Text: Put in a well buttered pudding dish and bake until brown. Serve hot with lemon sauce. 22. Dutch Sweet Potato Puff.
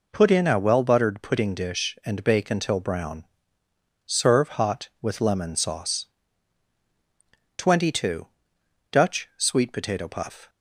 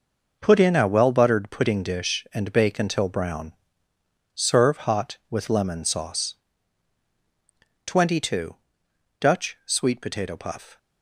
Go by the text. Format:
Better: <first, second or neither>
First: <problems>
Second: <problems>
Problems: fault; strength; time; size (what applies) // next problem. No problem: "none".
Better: first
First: none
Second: gets quieter; strong; throughout; 9 dB